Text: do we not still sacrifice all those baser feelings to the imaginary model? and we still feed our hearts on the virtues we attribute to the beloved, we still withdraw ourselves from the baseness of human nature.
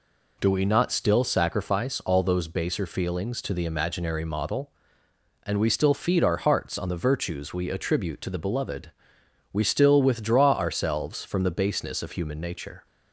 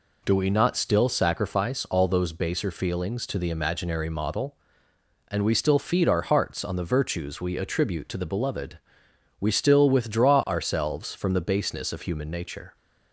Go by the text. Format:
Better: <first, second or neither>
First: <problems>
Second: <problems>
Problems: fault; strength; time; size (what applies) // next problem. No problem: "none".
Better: neither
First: none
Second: none